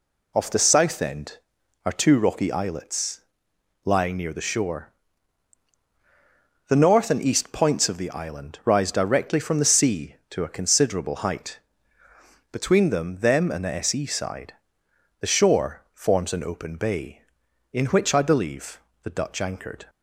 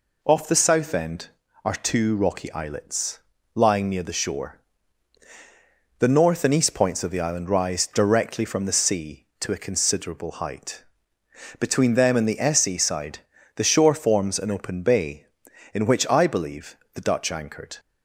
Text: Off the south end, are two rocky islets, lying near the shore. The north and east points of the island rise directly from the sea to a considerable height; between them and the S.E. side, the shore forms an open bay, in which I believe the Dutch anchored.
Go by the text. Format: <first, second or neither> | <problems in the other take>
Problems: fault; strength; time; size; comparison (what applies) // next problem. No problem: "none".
second | says "them" twice; at 13.2 s // pauses between "believe" and "the"; slight; at 18.7 s; 0.22 s long; slight in the second